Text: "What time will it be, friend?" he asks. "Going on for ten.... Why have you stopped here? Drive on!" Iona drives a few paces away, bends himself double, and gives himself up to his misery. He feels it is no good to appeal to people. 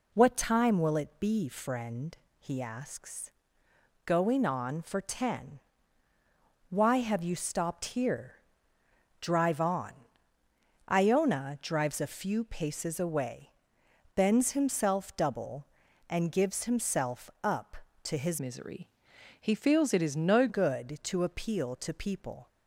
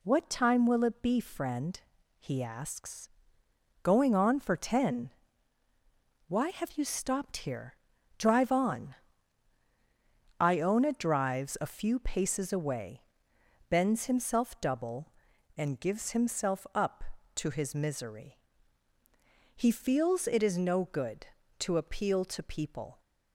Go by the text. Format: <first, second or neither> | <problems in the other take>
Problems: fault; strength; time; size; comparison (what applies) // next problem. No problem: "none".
second | changes voice from "misery" to "no"; from 18.3 to 20.4 s; 2.1 s long